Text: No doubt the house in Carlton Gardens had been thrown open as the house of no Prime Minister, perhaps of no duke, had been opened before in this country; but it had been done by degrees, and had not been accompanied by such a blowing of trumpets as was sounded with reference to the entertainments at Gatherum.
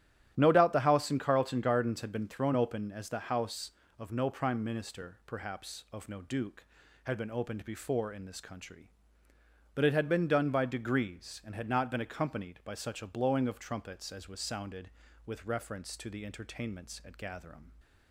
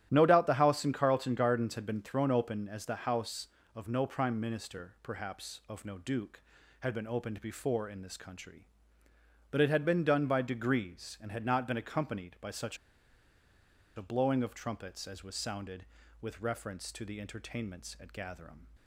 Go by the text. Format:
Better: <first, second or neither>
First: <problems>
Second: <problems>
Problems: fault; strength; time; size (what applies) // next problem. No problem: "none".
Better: first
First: starts louder than the rest; strong; until 1.3 s; 12 dB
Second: starts louder than the rest; strong; until 1.1 s; 12 dB // pauses between "such" and "a"; at 12.7 s; 1.1 s long